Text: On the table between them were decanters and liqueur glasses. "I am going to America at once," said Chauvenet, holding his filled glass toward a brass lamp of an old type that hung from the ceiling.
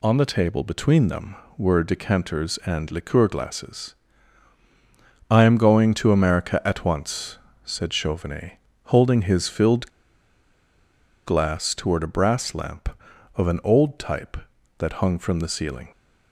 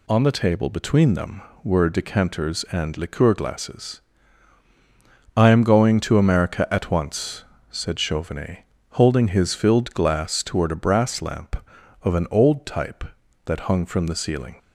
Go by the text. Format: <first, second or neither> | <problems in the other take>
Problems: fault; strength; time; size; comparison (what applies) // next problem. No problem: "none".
second | pauses between "filled" and "glass"; strong; at 9.8 s; 1.3 s long